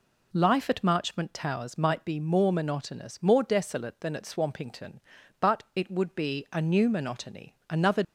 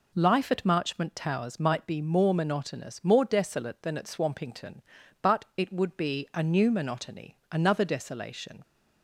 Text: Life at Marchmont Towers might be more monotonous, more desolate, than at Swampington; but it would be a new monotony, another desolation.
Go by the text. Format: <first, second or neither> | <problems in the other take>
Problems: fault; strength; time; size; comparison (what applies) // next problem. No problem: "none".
second | stops before "desolation"; at 8.0 s